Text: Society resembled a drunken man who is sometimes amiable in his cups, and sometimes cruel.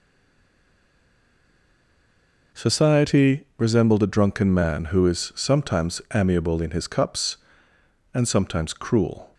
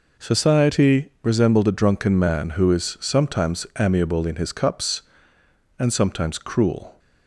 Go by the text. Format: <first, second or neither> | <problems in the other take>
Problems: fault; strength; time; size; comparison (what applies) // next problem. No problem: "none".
second | stays silent before the first word; strong; until 2.5 s; 2.5 s long